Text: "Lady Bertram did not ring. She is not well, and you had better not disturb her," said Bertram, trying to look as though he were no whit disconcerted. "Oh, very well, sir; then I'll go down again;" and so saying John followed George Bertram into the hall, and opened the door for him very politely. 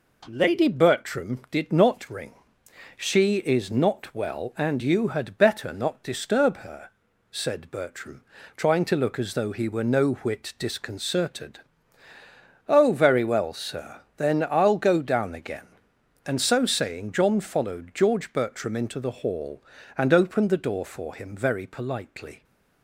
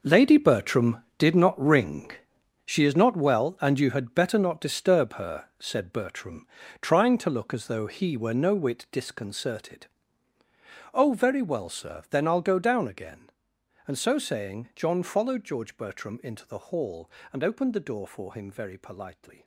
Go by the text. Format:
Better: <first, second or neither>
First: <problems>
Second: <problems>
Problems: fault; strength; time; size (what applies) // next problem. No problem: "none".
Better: first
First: none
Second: gets quieter; strong; throughout; 13 dB